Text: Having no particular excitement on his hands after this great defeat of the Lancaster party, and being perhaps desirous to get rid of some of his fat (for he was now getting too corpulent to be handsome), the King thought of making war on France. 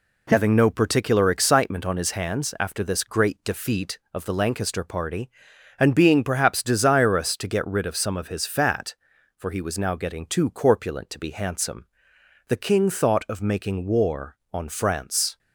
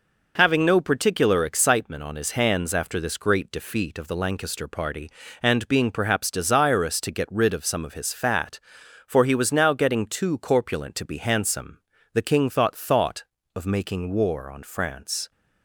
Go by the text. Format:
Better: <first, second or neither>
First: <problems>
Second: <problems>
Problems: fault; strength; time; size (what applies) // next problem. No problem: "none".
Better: first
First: none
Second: says "thought" twice; at 12.7 s